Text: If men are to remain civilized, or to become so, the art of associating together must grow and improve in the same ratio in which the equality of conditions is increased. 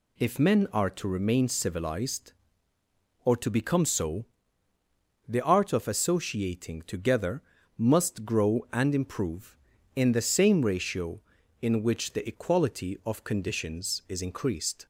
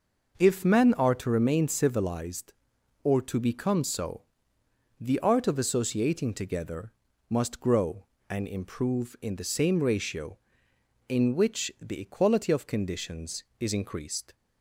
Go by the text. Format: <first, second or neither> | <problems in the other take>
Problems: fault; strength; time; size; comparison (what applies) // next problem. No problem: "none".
neither | pauses between "together" and "must"; the same in both